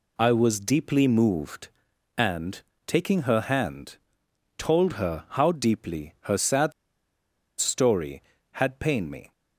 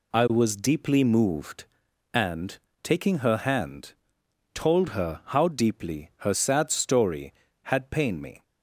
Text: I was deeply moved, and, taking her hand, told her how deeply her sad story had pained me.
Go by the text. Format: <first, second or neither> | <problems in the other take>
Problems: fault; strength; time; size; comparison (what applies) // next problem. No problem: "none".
second | pauses between "sad" and "story"; noticeable; at 6.7 s; 0.86 s long